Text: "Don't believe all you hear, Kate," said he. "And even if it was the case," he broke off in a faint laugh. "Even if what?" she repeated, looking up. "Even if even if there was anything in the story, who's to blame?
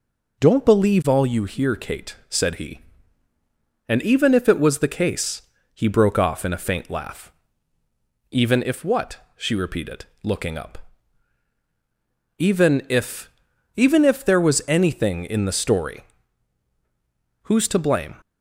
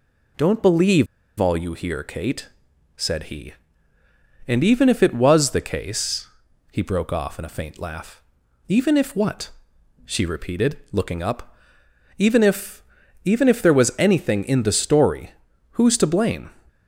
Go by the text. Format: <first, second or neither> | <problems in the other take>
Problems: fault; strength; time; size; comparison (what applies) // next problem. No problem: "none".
first | pauses between "believe" and "all"; slight; at 1.0 s; 0.33 s long // pauses between "if" and "even"; at 12.8 s; 0.42 s long; noticeable in the first